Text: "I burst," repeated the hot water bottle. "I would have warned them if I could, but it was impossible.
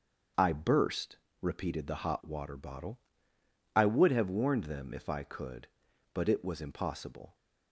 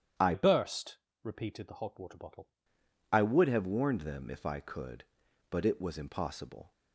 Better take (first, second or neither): first